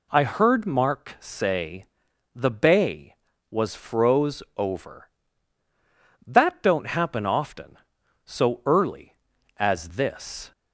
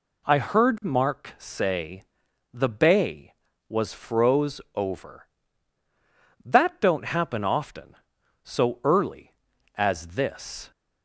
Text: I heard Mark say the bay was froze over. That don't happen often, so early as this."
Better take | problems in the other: neither | pauses between "say" and "the"; noticeable; the same in both

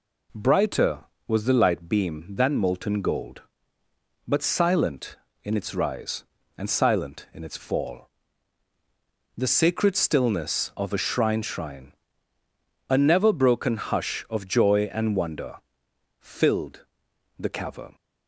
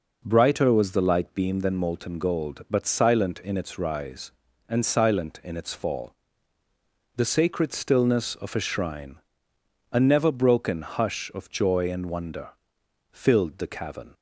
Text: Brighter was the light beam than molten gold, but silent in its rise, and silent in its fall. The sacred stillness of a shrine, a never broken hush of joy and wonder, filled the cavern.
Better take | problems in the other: second | says "shrine" twice; at 11.4 s // pauses between "filled" and "the"; noticeable; at 16.8 s; 0.52 s long

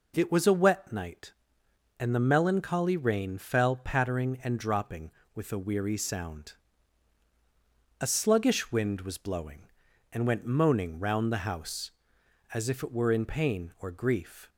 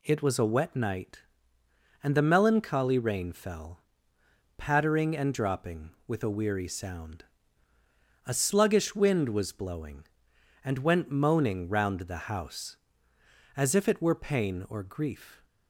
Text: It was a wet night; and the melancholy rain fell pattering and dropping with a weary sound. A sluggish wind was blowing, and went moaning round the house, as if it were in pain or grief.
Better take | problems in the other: first | pauses between "fell" and "pattering"; noticeable; at 3.8 s; 0.76 s long // skips "in"; at 14.1 s

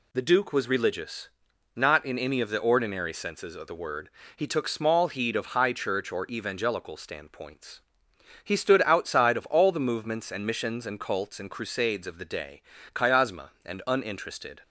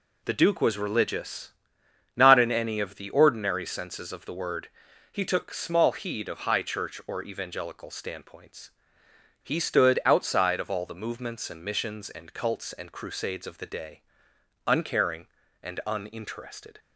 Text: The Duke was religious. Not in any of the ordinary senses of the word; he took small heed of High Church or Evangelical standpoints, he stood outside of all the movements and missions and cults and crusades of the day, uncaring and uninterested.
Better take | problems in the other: second | says "chiasma" for "uncaring"; at 12.9 s

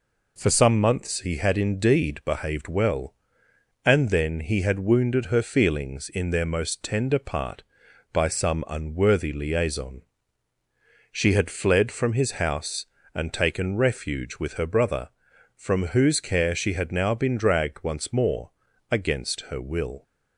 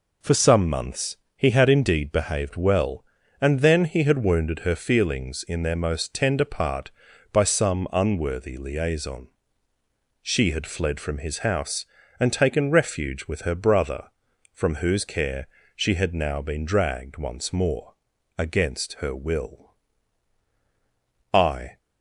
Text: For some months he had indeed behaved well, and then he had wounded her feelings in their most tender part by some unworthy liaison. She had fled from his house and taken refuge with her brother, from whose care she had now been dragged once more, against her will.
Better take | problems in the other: first | pauses between "months" and "he"; slight; at 1.1 s; 0.18 s long // pauses between "care" and "she"; slight; at 15.4 s; 0.26 s long // goes on to say "I"; slight; from 21.3 s on; 0.44 s long

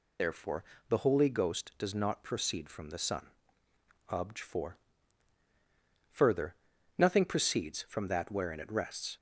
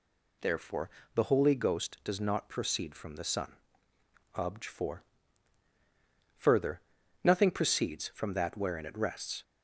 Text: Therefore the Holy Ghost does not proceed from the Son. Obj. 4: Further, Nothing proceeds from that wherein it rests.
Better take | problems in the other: second | loses the start of "Therefore"; at 0.1 s; 50 ms // pauses between "Therefore" and "the"; slight; at 0.6 s; 0.26 s long; slight in the second

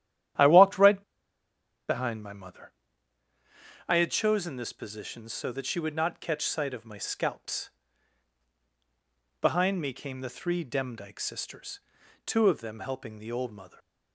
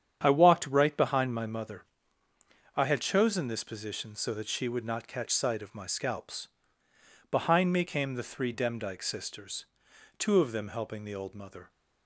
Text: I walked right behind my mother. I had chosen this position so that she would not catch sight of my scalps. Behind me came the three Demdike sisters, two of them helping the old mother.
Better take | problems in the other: second | starts louder than the rest; strong; until 2.2 s; 11 dB; strong in the second // pauses between "right" and "behind"; noticeable; at 1.0 s; 0.86 s long

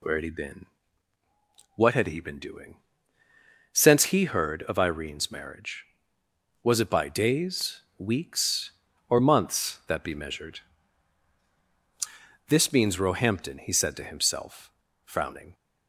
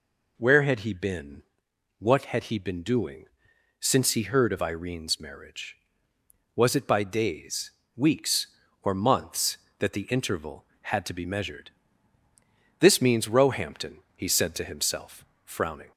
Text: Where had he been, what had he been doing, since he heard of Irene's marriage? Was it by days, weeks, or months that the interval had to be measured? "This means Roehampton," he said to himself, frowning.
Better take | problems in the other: second | skips "the interval had to"; at 10.0 s

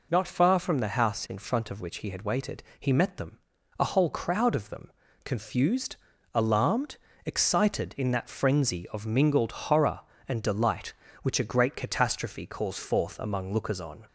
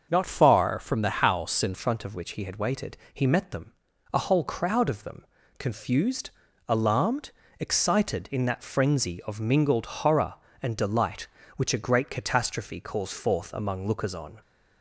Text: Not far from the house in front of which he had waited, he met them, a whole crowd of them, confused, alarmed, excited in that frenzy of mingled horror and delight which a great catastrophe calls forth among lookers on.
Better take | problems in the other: first | starts louder than the rest; until 1.1 s; 6.5 dB // changes voice from "far" to "in"; from 0.2 to 1.7 s; 1.5 s long

